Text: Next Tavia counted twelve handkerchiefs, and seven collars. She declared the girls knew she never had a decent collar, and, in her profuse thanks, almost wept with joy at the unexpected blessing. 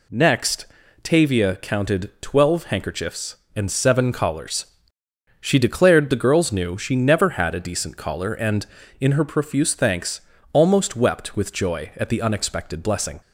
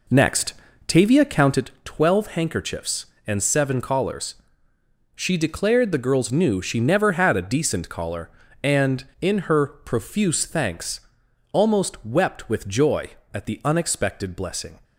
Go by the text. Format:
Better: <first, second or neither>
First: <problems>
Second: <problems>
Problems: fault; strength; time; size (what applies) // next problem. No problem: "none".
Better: first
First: pauses between "Next" and "Tavia"; at 0.6 s; 0.38 s long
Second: starts louder than the rest; until 1.7 s; 3.5 dB // pauses between "Next" and "Tavia"; slight; at 0.5 s; 0.32 s long